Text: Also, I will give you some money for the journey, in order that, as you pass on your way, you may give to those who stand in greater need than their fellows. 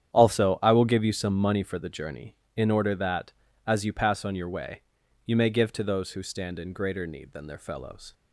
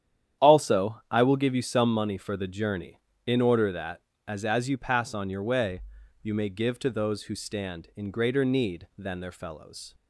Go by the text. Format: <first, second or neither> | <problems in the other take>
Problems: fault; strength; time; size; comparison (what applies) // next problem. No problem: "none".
first | starts louder than the rest; strong; until 1.5 s; 9.5 dB; strong in the first // says "as" twice; at 4.4 s